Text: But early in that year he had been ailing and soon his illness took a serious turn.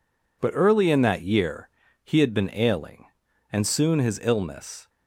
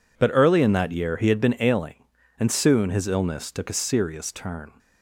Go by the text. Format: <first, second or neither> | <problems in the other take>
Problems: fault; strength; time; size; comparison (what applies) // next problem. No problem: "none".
second | pauses between "year" and "he"; slight; at 1.6 s; 0.34 s long // stops before "took a serious turn"; at 4.8 s